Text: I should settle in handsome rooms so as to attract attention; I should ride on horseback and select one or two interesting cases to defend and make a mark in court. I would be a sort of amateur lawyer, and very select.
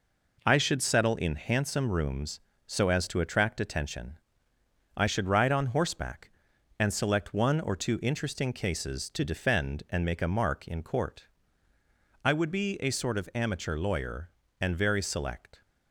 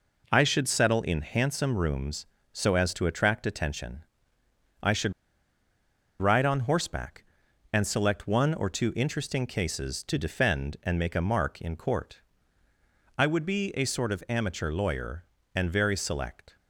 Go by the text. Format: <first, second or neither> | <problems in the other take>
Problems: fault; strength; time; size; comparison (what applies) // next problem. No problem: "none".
first | pauses between "should" and "ride"; at 5.1 s; 1.0 s long